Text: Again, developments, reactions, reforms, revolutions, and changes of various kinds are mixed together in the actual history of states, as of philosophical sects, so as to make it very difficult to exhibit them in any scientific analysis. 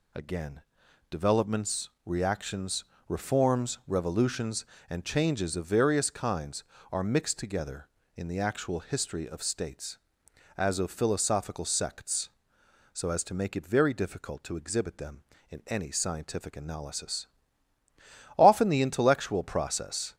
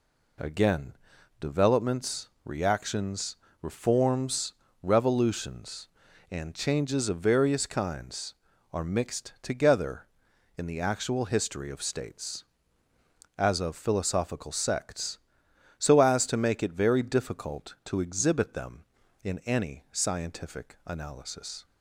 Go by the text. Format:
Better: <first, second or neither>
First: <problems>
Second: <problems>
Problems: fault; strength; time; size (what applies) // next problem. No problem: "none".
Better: second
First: goes on to say "Often the intellectual process"; strong; from 18.3 s on; 1.7 s long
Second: none